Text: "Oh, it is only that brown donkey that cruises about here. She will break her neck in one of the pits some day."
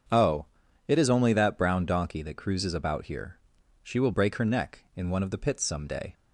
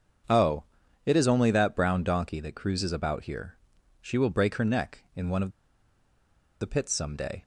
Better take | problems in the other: first | starts louder than the rest; until 1.7 s; 7 dB; also in the first // pauses between "of" and "the"; at 5.5 s; 1.0 s long

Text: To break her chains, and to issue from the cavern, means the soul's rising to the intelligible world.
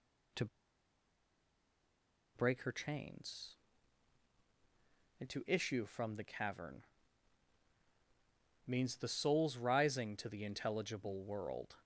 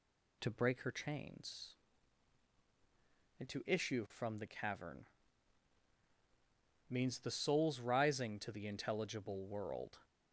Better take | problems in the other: second | pauses between "To" and "break"; strong; at 0.4 s; 1.9 s long

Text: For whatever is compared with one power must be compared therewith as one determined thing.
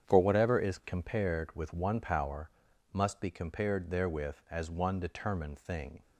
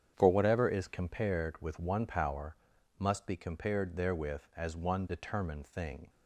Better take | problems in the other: neither | starts louder than the rest; strong; the same in both // pauses between "power" and "must"; the same in both

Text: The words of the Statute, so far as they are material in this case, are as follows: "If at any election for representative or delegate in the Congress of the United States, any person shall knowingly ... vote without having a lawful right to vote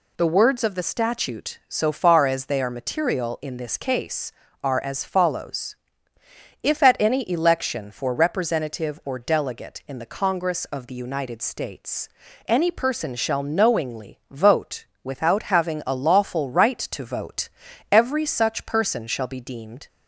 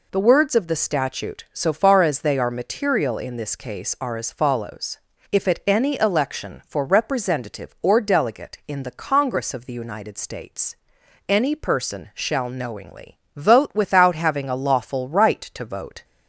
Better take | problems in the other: second | pauses between "vote" and "without"; slight; at 14.8 s; 0.18 s long // goes on to say "every such person shall be deemed"; strong; from 17.9 s on; 1.9 s long

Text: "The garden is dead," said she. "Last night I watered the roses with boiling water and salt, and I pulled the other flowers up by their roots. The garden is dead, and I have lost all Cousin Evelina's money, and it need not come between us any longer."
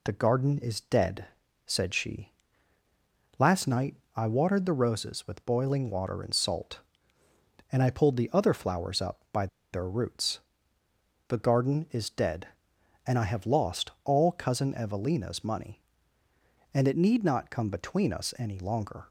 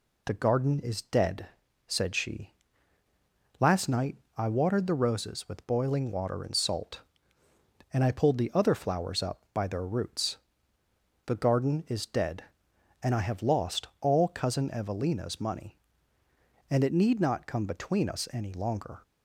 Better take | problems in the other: second | pauses between "night" and "I"; slight; at 3.9 s; 0.22 s long; slight in the second // pauses between "by" and "their"; slight; at 9.4 s; 0.26 s long

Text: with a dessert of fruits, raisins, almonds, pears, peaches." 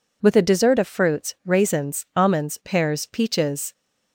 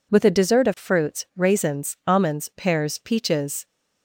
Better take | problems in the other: neither | none

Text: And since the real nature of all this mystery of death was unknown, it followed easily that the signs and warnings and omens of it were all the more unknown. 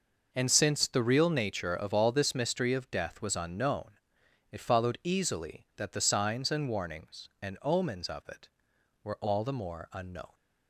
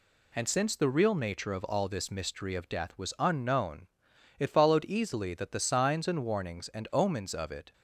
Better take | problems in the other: first | stops before "were all the more unknown"; at 7.7 s

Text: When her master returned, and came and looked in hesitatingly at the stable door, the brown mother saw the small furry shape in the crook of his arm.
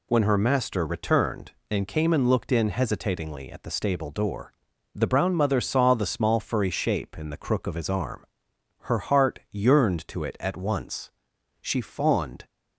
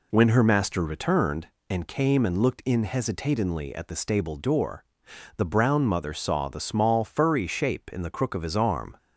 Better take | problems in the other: second | goes on to say "Her heart yearned to it at once She fawned"; strong; from 8.8 s on; 3.6 s long

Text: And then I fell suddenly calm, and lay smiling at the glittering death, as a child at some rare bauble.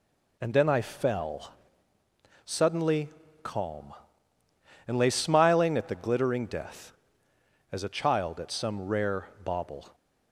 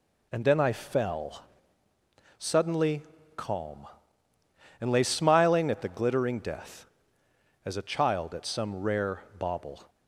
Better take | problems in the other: neither | pauses between "fell" and "suddenly"; noticeable; the same in both // pauses between "suddenly" and "calm"; slight; the same in both

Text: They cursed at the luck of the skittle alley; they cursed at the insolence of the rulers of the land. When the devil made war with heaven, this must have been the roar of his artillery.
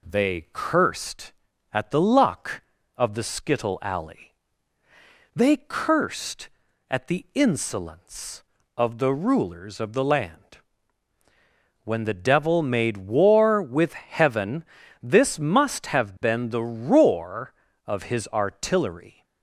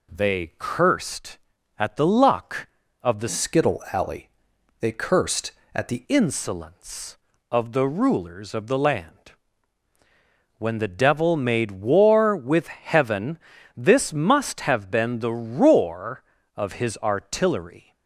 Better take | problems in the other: first | changes voice from "skittle" to "the"; from 3.2 to 6.0 s; 2.8 s long

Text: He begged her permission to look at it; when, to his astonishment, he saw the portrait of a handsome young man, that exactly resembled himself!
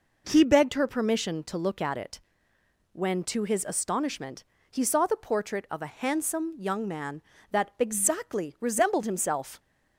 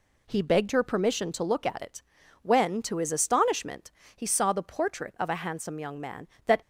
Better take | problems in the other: first | stops before "exactly resembled himself"; at 6.6 s

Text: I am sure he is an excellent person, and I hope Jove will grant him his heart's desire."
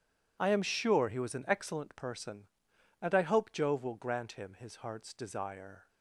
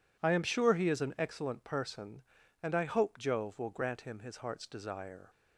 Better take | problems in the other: second | says "was" for "is"; at 1.1 s

